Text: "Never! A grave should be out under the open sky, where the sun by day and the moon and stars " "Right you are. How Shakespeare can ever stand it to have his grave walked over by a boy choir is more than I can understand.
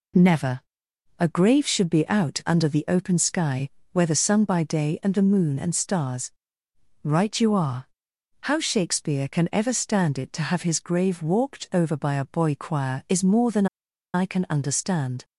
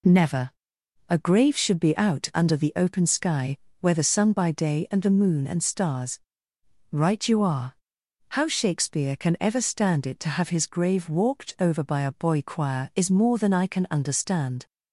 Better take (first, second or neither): second